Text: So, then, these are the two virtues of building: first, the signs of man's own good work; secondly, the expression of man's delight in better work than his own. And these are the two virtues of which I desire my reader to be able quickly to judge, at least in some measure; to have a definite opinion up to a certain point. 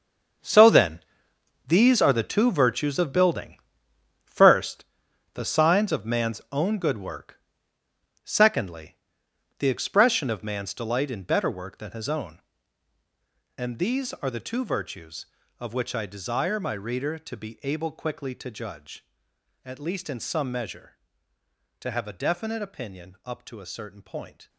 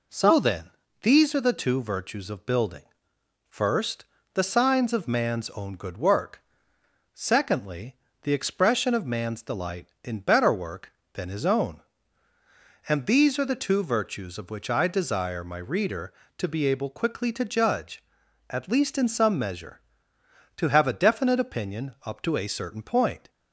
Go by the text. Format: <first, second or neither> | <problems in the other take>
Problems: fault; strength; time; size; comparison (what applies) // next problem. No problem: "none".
second | gets quieter; strong; throughout; 12.5 dB